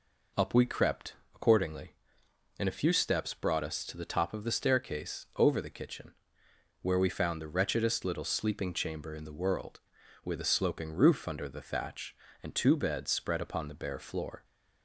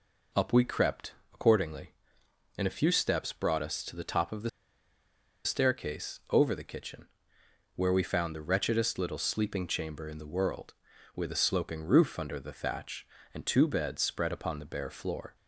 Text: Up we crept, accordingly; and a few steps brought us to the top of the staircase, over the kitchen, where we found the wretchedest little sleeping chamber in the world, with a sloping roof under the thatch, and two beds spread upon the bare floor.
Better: first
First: none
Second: pauses between "the" and "staircase"; noticeable; at 4.4 s; 0.96 s long

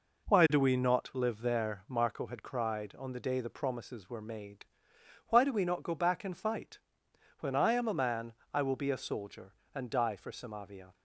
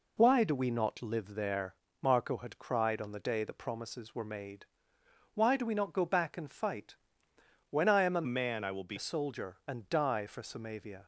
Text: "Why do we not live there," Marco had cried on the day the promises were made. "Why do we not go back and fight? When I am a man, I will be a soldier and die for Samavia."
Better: first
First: none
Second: changes voice from "man" to "be"; from 8.2 to 8.9 s; 0.7 s long

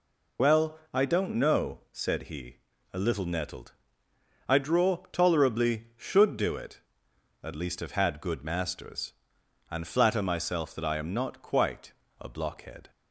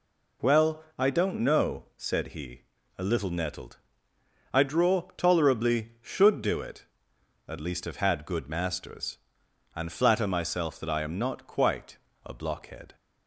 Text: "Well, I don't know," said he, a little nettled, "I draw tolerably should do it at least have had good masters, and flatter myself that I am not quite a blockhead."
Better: second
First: loses the start of "Well"; at 0.3 s; 30 ms // pauses between "quite" and "a"; slight; at 11.9 s; 0.26 s long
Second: pauses between "quite" and "a"; slight; at 11.9 s; 0.26 s long

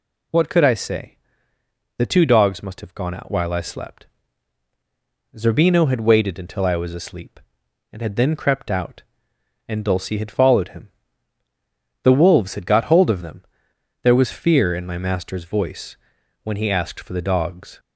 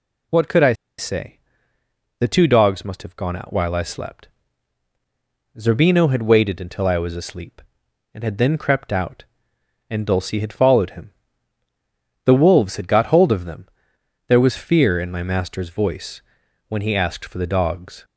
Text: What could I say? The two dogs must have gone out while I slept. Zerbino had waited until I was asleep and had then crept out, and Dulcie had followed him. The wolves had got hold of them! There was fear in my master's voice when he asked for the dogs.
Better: first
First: pauses between "voice" and "when"; noticeable; at 15.9 s; 0.48 s long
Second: pauses between "I" and "say"; slight; at 0.7 s; 0.24 s long // pauses between "voice" and "when"; noticeable; at 16.2 s; 0.48 s long

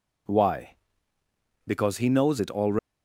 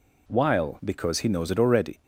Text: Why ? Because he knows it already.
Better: first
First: none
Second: says "While" for "Why"; at 0.2 s

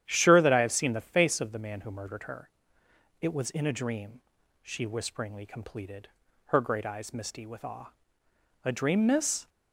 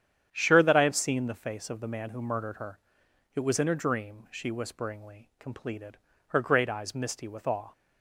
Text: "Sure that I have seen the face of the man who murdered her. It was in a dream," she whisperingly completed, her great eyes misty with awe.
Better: second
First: starts louder than the rest; strong; until 1.0 s; 10.5 dB // goes on to say "A dream Miss"; noticeable; from 8.6 s on; 0.86 s long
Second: starts louder than the rest; strong; until 1.3 s; 9 dB

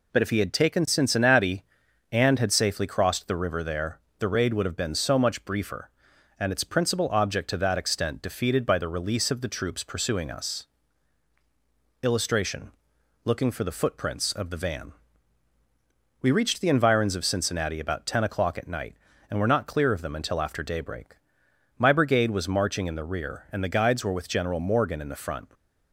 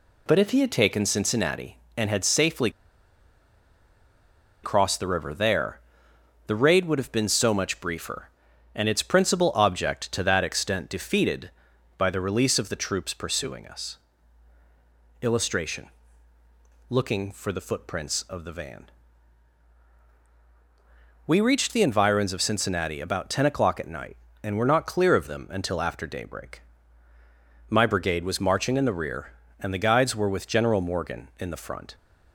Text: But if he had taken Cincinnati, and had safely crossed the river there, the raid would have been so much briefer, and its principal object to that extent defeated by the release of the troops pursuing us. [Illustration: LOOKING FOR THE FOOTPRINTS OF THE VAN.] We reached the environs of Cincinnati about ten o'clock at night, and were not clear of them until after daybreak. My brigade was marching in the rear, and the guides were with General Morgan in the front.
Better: first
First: none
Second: pauses between "safely" and "crossed"; strong; at 2.6 s; 1.9 s long

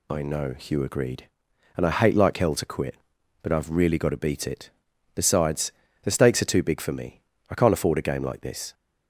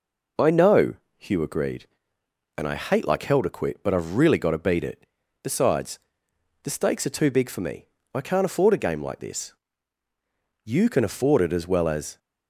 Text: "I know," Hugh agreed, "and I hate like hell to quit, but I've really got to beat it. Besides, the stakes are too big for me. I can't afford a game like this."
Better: first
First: none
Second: goes on to say "You can afford it as well as"; from 10.6 s on; 1.5 s long

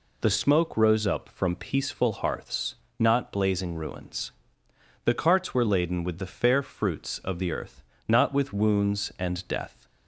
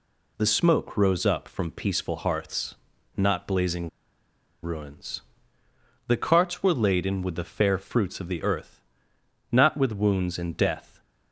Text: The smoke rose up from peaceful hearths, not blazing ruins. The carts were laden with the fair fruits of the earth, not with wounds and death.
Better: first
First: none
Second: pauses between "blazing" and "ruins"; noticeable; at 3.8 s; 0.74 s long

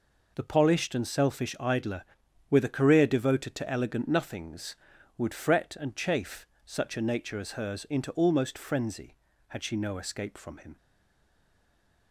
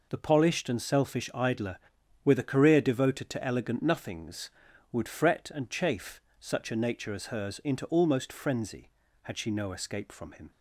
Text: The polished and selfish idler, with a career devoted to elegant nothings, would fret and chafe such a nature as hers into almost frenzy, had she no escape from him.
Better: second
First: pauses between "chafe" and "such"; slight; at 6.4 s; 0.18 s long // stays silent after the last word; noticeable; from 10.7 s on; 1.4 s long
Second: pauses between "chafe" and "such"; slight; at 6.2 s; 0.18 s long

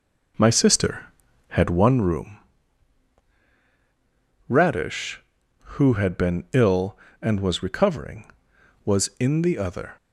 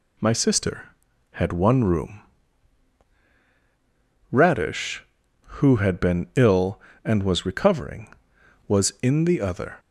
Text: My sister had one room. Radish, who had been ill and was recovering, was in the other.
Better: second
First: starts louder than the rest; noticeable; until 2.0 s; 5 dB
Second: none

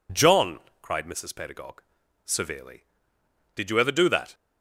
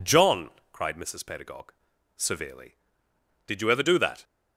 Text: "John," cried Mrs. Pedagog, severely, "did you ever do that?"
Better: neither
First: none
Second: none

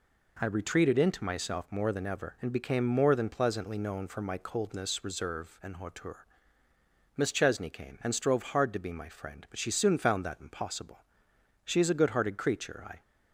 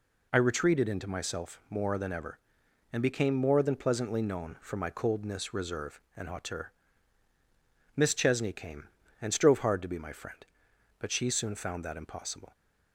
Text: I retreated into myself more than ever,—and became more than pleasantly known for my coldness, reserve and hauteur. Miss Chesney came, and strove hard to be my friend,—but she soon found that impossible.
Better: second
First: goes on to say "She is a good hearted creature I"; from 11.6 s on; 1.3 s long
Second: none

